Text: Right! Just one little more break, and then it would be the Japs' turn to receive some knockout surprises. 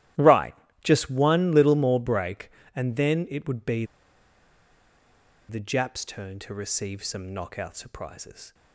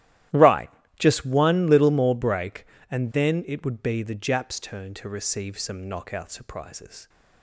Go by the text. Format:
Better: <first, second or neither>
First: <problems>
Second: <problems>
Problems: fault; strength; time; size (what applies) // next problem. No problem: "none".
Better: second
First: starts louder than the rest; strong; until 1.4 s; 14 dB // pauses between "be" and "the"; strong; at 3.8 s; 1.6 s long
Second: starts louder than the rest; strong; until 1.6 s; 14 dB